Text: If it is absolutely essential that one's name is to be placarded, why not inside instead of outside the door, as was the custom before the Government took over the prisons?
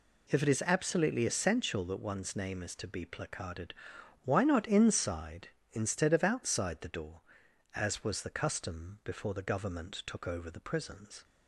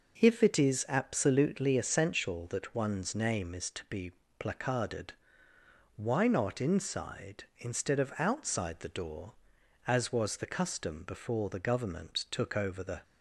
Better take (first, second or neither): first